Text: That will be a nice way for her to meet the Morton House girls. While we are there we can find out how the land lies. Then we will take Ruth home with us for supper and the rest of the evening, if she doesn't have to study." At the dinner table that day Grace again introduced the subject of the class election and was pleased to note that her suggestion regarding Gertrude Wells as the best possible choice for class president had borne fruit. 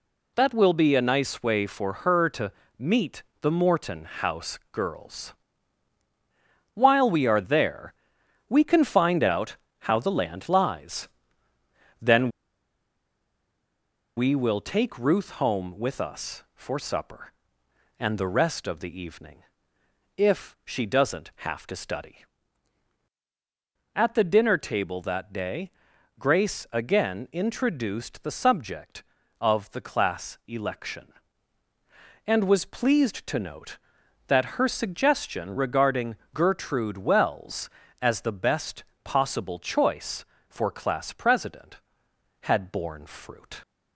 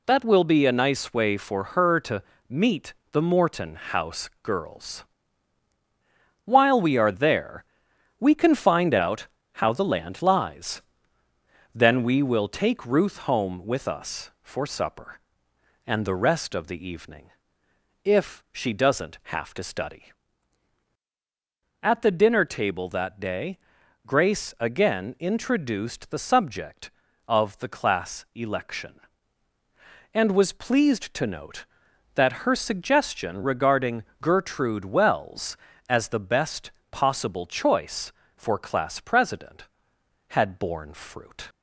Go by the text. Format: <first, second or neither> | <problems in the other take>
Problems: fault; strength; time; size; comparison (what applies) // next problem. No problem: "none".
second | pauses between "to" and "meet"; slight; at 2.5 s; 0.26 s long; slight in the second // pauses between "meet" and "the"; slight; at 3.2 s; 0.20 s long; slight in the second // pauses between "there" and "we"; noticeable; at 7.9 s; 0.54 s long; noticeable in the second // pauses between "out" and "how"; slight; at 9.5 s; 0.24 s long; slight in the second // pauses between "Then" and "we"; strong; at 12.2 s; 1.8 s long // pauses between "day" and "Grace"; noticeable; at 25.6 s; 0.48 s long; noticeable in the second // pauses between "regarding" and "Gertrude"; slight; at 36.1 s; 0.18 s long; slight in the second // pauses between "best" and "possible"; slight; at 38.8 s; 0.20 s long; slight in the second